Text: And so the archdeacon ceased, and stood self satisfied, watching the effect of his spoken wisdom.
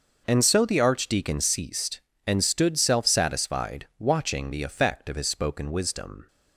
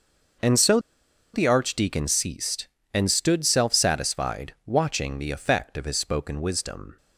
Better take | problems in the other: first | pauses between "so" and "the"; noticeable; at 0.7 s; 0.55 s long

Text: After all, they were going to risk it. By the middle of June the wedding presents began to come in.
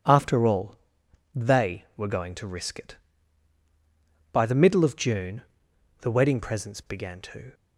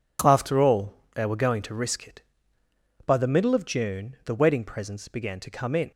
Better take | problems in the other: second | pauses between "June" and "the"; noticeable; at 5.4 s; 0.58 s long // stops before "come in"; at 7.5 s

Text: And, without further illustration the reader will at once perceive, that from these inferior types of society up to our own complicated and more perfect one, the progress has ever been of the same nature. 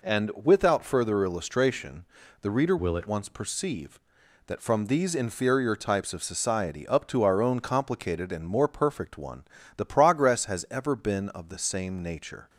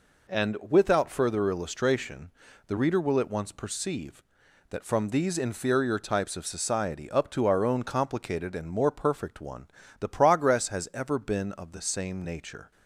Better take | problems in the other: second | pauses between "illustration" and "the"; slight; at 2.0 s; 0.36 s long; slight in the second // changes voice from "will" to "at"; from 2.7 to 3.0 s; 0.3 s long

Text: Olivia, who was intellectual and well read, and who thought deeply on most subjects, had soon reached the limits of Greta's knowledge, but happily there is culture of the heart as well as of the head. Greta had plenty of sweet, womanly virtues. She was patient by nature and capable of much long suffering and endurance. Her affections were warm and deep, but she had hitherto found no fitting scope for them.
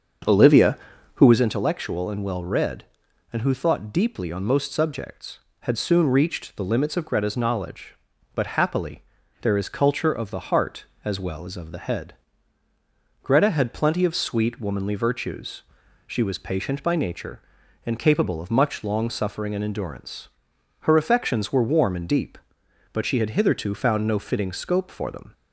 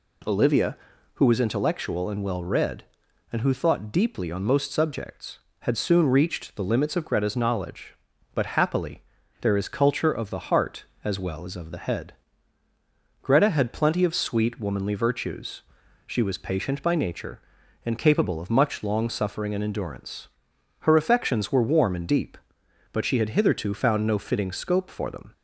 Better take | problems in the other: second | starts louder than the rest; until 1.6 s; 6.5 dB // pauses between "happily" and "there"; at 9.0 s; 0.40 s long; also in the second

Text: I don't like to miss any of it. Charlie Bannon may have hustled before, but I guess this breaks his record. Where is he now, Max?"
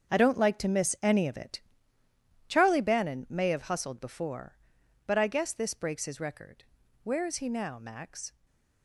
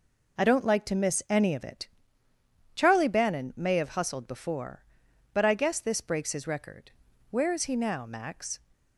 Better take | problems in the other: second | gets quieter; strong; throughout; 12.5 dB // stays silent after the last word; slight; from 8.2 s on; 0.6 s long

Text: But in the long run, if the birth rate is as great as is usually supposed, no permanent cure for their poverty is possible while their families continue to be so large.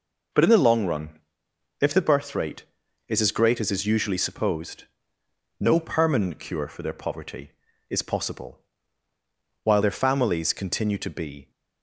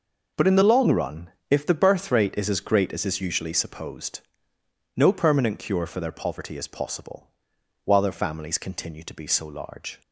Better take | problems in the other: second | pauses between "possible" and "while"; at 8.5 s; 1.0 s long; noticeable in the second // stops before "so large"; at 11.5 s

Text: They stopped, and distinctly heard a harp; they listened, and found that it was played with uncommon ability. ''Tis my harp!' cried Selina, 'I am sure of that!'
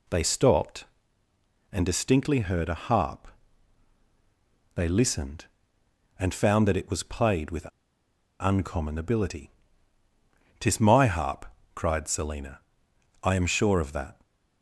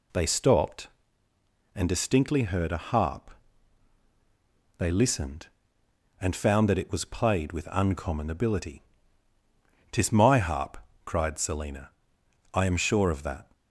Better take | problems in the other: second | pauses between "with" and "uncommon"; noticeable; at 7.6 s; 0.72 s long

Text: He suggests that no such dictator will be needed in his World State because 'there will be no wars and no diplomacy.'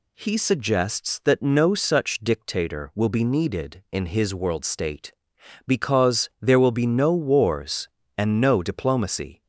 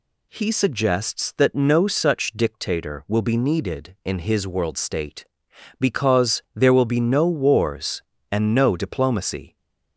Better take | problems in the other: neither | none

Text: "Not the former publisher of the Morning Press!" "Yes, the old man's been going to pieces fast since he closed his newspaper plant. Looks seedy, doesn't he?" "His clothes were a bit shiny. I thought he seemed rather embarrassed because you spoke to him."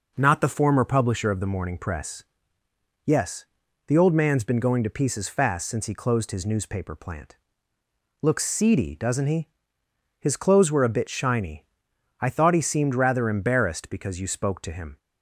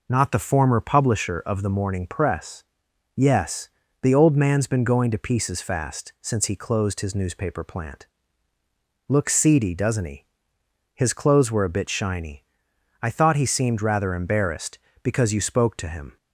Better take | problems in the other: neither | none

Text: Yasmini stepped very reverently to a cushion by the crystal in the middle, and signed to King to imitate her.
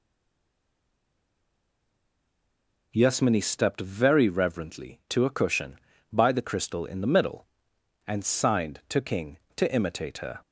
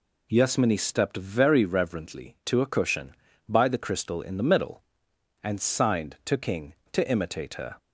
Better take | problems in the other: second | stays silent before the first word; strong; until 2.9 s; 2.9 s long

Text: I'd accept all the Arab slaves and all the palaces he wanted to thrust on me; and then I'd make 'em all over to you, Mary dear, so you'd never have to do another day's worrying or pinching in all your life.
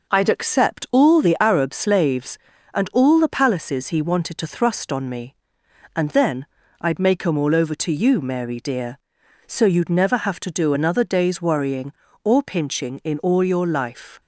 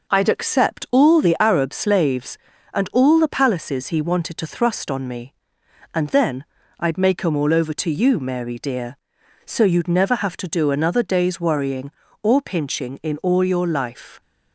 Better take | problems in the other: neither | pauses between "then" and "I'd"; slight; the same in both

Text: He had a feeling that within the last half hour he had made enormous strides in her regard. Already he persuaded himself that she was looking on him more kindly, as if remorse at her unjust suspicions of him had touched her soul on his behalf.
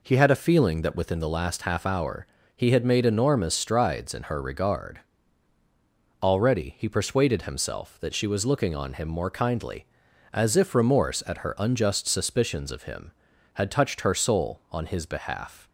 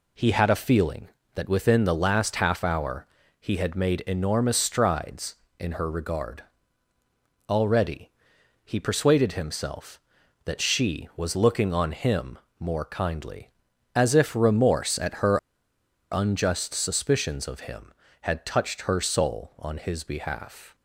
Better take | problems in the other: first | pauses between "hour" and "he"; slight; at 3.0 s; 0.34 s long; slight in the first // pauses between "Already" and "he"; noticeable; at 8.0 s; 0.56 s long // pauses between "him" and "more"; slight; at 12.3 s; 0.20 s long // pauses between "her" and "unjust"; noticeable; at 15.3 s; 0.74 s long

